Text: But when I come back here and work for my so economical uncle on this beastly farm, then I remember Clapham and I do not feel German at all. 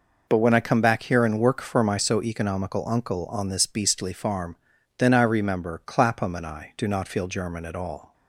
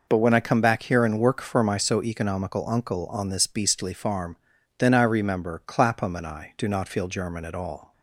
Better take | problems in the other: neither | none

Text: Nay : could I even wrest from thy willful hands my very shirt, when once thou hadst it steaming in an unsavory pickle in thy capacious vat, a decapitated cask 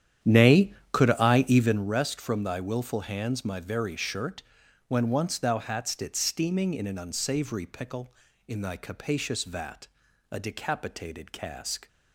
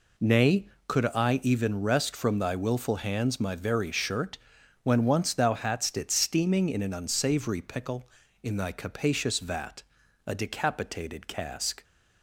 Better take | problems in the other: second | starts louder than the rest; strong; until 2.0 s; 10 dB

